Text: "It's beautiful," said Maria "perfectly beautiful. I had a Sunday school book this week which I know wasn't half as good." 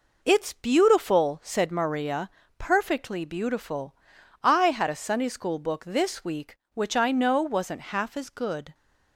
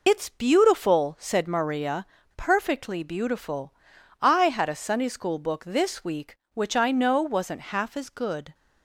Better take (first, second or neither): first